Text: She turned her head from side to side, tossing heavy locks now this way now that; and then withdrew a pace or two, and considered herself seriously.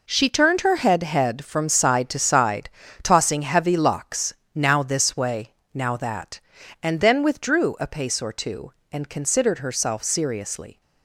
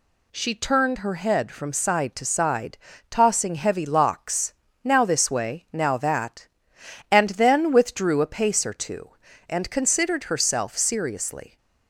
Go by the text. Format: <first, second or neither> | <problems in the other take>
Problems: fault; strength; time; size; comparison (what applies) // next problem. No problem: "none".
second | says "head" twice; at 1.0 s // pauses between "locks" and "now"; slight; at 4.3 s; 0.20 s long; slight in the second // pauses between "way" and "now"; slight; at 5.5 s; 0.18 s long